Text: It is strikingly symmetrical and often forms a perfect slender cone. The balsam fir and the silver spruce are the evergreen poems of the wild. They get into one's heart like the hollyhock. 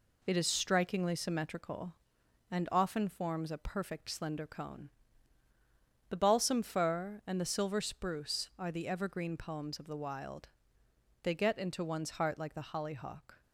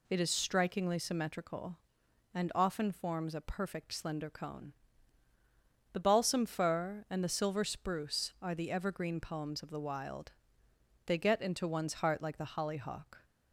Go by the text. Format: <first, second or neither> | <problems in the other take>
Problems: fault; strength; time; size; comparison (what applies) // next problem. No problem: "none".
second | gets quieter; noticeable; throughout; 5 dB